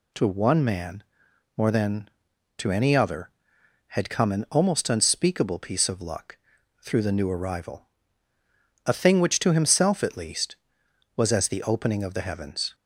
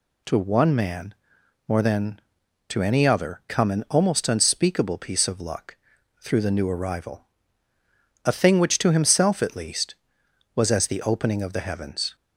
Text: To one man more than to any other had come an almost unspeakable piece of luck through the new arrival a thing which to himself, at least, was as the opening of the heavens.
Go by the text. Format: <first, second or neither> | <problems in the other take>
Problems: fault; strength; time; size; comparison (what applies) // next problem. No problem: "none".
first | pauses between "man" and "more"; noticeable; at 1.1 s; 0.54 s long; noticeable in the first // skips "had"; at 3.4 s // pauses between "luck" and "through"; noticeable; at 5.7 s; 0.46 s long; noticeable in the first // pauses between "arrival" and "a"; at 7.2 s; 1.0 s long; also in the first